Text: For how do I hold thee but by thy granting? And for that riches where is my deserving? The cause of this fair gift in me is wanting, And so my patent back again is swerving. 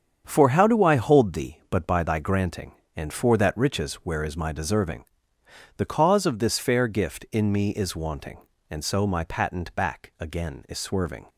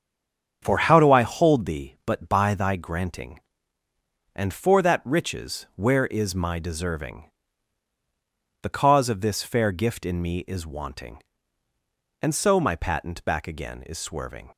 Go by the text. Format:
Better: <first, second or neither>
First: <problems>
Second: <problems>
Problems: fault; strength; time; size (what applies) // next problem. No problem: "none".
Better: first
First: starts louder than the rest; strong; until 1.2 s; 7.5 dB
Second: stays silent before the first word; slight; until 0.6 s; 0.6 s long // starts louder than the rest; strong; until 1.6 s; 7.5 dB